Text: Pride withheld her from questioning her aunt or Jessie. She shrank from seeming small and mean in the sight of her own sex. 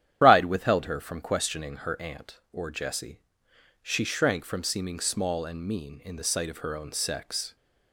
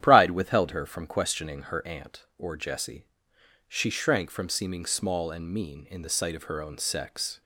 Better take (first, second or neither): second